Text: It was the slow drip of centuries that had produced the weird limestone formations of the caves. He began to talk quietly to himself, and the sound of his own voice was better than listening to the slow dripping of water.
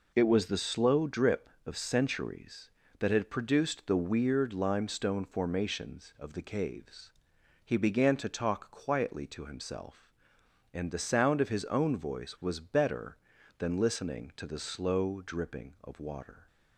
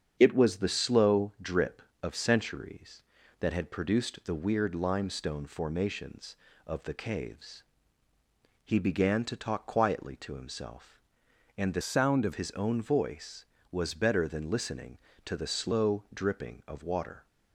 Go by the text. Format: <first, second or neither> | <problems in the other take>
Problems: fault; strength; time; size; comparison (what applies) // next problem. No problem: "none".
first | starts louder than the rest; strong; until 1.2 s; 7.5 dB // changes voice from "sound" to "of"; from 11.8 to 12.3 s; 0.5 s long